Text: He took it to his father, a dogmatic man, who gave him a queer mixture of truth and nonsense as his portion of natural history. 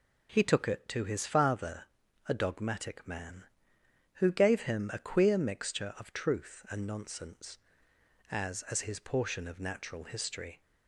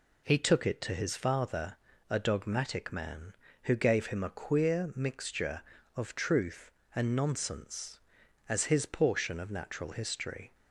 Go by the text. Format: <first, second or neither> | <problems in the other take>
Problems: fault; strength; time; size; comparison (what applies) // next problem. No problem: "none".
second | says "as" twice; at 8.7 s